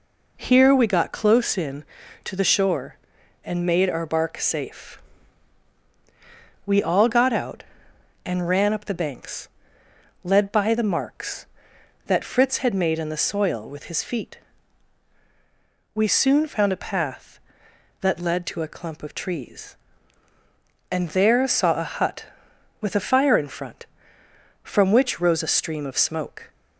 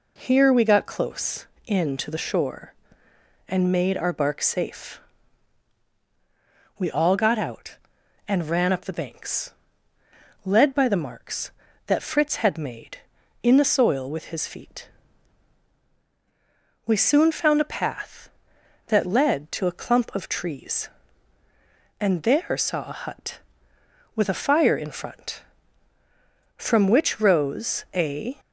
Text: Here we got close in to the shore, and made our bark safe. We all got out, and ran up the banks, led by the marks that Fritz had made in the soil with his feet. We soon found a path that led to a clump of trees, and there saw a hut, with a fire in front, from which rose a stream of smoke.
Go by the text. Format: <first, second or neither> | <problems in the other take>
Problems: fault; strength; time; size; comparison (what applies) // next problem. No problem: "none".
first | stops before "stream of smoke"; at 28.3 s